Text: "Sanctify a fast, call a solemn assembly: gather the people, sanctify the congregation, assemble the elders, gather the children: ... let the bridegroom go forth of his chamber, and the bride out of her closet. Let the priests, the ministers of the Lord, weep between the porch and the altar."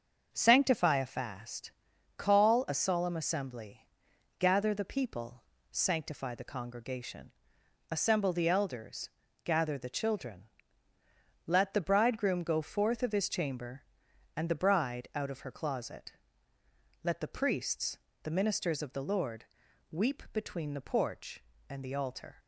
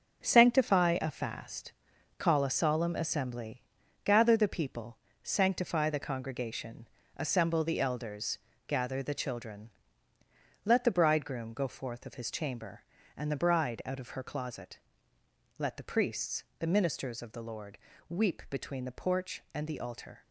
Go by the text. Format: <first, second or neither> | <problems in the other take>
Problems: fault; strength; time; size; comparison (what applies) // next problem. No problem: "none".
first | gets quieter; strong; throughout; 8 dB // starts louder than the rest; until 1.2 s; 6.5 dB; also in the first